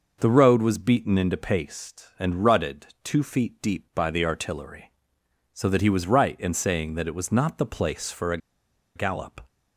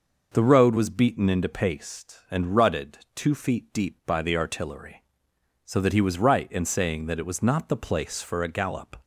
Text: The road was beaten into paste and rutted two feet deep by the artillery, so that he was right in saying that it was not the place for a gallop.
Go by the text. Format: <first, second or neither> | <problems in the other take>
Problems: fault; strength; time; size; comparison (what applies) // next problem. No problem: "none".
second | pauses between "rutted" and "two"; slight; at 2.8 s; 0.18 s long; slight in the second // pauses between "a" and "gallop"; noticeable; at 8.3 s; 0.58 s long